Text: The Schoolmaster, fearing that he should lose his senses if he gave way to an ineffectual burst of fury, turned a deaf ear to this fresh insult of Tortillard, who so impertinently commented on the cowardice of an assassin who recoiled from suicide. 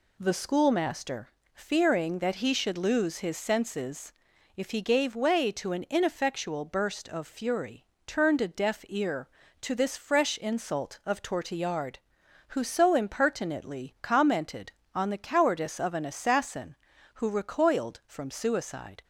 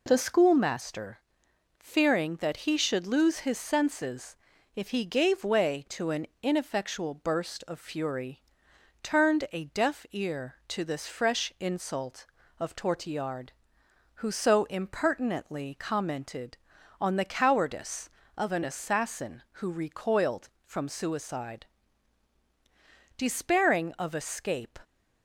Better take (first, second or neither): first